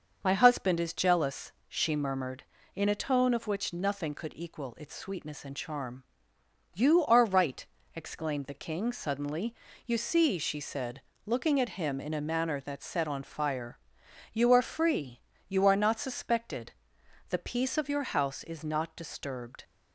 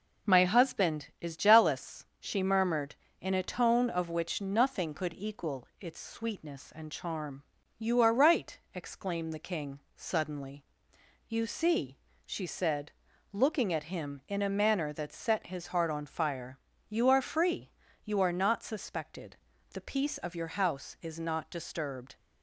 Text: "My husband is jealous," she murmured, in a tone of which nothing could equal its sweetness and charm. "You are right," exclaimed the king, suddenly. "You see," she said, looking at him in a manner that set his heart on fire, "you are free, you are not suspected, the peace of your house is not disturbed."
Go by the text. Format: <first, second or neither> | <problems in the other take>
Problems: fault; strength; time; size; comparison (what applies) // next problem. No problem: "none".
second | starts louder than the rest; until 1.2 s; 6.5 dB // skips "his heart"; at 13.0 s